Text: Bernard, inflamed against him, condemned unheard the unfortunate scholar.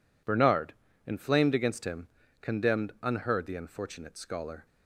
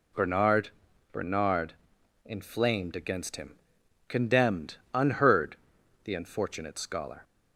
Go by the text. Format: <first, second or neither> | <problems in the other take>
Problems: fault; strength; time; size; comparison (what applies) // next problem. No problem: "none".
first | says "Bernard" twice; at 1.1 s // pauses between "condemned" and "unheard"; slight; at 4.7 s; 0.16 s long // pauses between "unheard" and "the"; noticeable; at 5.5 s; 0.48 s long